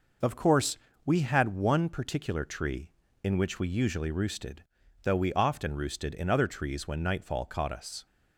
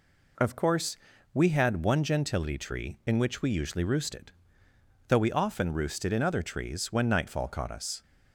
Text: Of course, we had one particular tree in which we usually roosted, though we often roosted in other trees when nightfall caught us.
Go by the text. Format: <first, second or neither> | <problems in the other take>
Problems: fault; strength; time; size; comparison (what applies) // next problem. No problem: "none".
first | says "gentility" for "particular"; at 2.0 s